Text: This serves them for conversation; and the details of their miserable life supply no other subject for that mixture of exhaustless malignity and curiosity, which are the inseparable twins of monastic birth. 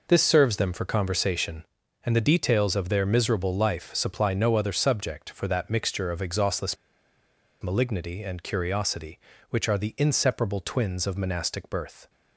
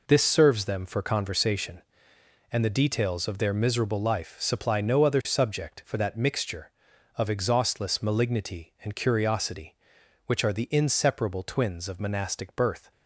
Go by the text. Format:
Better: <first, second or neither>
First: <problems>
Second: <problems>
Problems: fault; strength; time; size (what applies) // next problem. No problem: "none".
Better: second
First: pauses between "exhaustless" and "malignity"; noticeable; at 6.7 s; 0.87 s long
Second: none